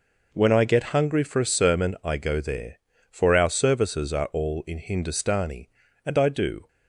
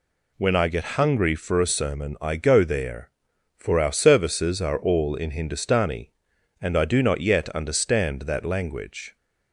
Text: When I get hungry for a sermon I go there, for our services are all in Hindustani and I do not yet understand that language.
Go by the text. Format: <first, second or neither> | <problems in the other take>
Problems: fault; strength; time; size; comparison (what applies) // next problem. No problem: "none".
second | stops before "not yet understand that language"; at 6.6 s